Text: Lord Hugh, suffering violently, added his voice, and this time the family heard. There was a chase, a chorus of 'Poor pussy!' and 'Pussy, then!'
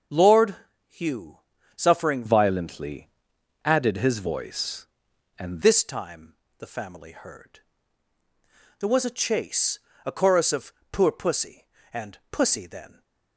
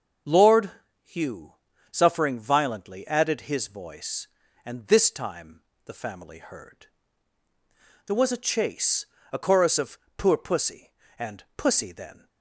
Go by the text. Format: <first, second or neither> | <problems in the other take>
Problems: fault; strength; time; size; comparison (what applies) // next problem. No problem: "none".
second | starts louder than the rest; until 1.8 s; 6.5 dB; also in the second // pauses between "Lord" and "Hugh"; slight; at 0.5 s; 0.34 s long; slight in the second // changes voice from "violently" to "and"; from 2.2 to 5.6 s; 3.4 s long // pauses between "time" and "the"; slight; at 6.3 s; 0.26 s long; slight in the second // pauses between "of" and "Poor"; slight; at 10.7 s; 0.20 s long; slight in the second